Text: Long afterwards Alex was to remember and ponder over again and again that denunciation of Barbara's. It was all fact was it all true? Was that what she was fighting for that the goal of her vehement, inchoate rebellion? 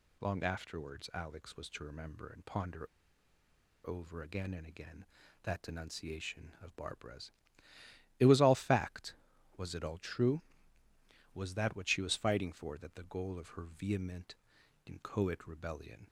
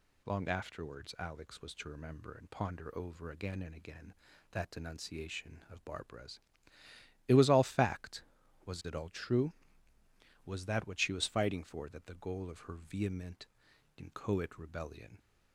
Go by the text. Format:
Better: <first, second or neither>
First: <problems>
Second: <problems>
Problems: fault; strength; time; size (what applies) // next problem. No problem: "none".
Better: second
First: pauses between "ponder" and "over"; at 2.8 s; 0.99 s long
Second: none